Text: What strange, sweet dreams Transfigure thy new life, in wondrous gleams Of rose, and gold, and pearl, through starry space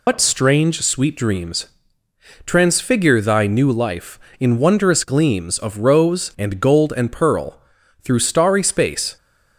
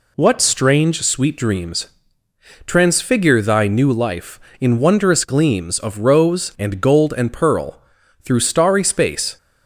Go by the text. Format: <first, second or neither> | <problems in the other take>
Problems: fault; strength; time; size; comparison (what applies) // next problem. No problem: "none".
second | loses the start of "What"; at 0.0 s; 130 ms // pauses between "dreams" and "Transfigure"; noticeable; at 1.6 s; 0.80 s long; noticeable in the second